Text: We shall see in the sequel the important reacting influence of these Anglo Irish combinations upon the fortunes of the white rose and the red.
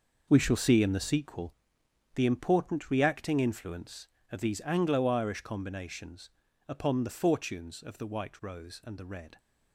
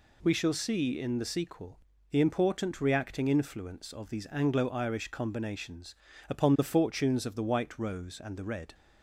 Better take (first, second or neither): second